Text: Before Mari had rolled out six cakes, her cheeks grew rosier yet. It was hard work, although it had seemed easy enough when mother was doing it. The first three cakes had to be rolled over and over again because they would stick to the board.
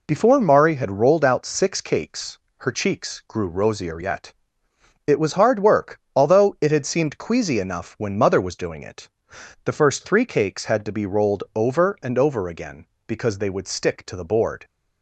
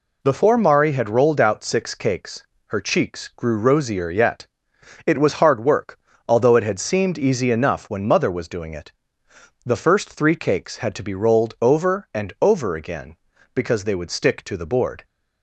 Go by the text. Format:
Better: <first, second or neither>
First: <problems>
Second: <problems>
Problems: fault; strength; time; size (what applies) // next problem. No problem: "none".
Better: second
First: says "queasy" for "easy"; at 7.1 s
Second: none